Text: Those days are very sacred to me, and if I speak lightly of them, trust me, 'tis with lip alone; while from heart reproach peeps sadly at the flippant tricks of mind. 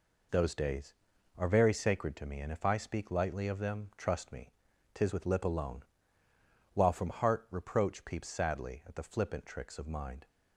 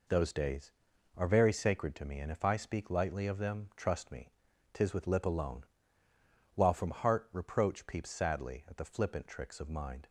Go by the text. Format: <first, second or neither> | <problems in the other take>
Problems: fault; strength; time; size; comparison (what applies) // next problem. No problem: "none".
neither | none